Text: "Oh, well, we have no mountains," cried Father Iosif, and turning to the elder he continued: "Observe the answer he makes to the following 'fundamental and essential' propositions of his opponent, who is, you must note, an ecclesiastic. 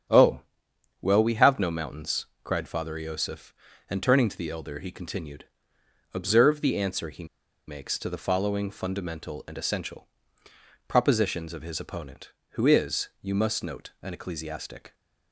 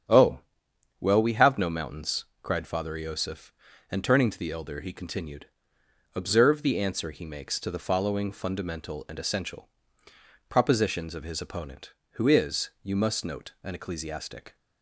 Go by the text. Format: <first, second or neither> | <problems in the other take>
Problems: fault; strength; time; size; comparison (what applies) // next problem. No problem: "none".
second | starts louder than the rest; strong; until 1.7 s; 8.5 dB; strong in the second // pauses between "he" and "makes"; at 7.2 s; 0.41 s long // pauses between "essential" and "propositions"; noticeable; at 10.0 s; 0.80 s long; noticeable in the second